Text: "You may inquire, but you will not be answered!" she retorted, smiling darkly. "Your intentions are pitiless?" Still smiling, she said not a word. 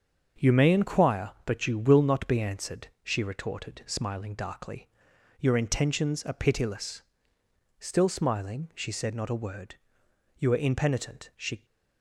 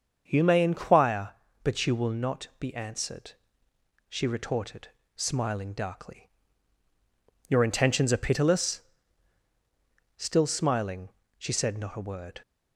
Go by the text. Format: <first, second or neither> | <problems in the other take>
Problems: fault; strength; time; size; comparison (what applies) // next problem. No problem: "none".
second | starts louder than the rest; until 1.5 s; 7 dB; also in the second // goes on to say "You are impenitent She"; noticeable; from 10.3 s on; 1.2 s long